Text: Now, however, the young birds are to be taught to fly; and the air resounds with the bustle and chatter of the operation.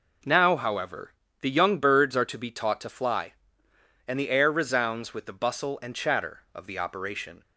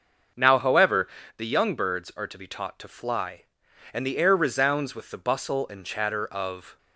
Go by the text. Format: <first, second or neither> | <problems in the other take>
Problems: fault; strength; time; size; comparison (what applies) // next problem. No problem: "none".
first | starts louder than the rest; until 1.6 s; 6 dB // stops before "the operation"; at 6.7 s